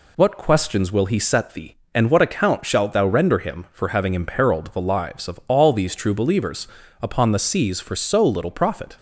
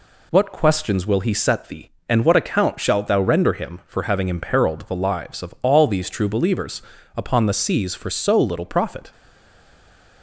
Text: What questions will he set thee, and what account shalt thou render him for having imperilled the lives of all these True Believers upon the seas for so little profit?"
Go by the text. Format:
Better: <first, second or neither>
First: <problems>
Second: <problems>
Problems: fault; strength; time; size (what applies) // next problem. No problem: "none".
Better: first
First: pauses between "Believers" and "upon"; slight; at 6.6 s; 0.34 s long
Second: pauses between "Believers" and "upon"; slight; at 6.8 s; 0.34 s long // stays silent after the last word; from 9.1 s on; 1.1 s long